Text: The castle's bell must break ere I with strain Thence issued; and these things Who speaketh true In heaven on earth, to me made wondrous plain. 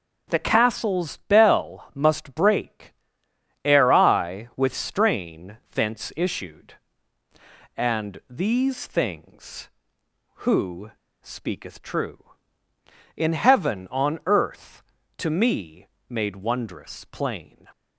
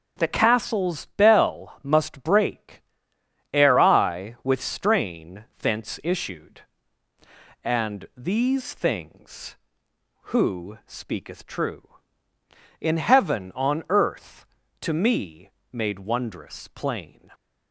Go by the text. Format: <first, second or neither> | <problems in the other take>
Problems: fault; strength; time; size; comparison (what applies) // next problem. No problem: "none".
second | pauses between "break" and "ere"; noticeable; at 2.9 s; 0.72 s long; noticeable in the second // pauses between "strain" and "Thence"; slight; at 5.5 s; 0.16 s long; slight in the second // pauses between "Who" and "speaketh"; slight; at 10.9 s; 0.31 s long // pauses between "me" and "made"; slight; at 15.8 s; 0.24 s long; slight in the second